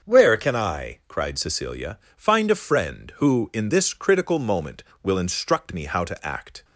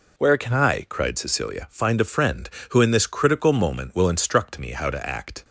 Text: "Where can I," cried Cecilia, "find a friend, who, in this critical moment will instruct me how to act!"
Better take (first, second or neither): second